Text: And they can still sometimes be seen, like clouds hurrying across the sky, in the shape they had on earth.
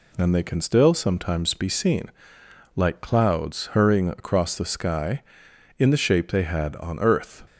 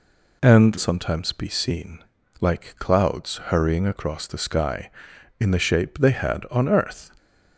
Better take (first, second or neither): first